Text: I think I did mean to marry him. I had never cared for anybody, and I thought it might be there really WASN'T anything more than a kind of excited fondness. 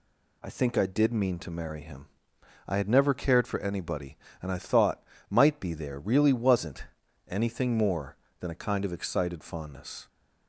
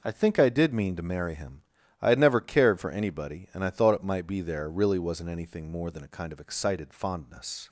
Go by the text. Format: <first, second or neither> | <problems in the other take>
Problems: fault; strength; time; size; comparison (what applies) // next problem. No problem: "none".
second | skips "it"; at 5.1 s // pauses between "WASN'T" and "anything"; at 6.8 s; 0.44 s long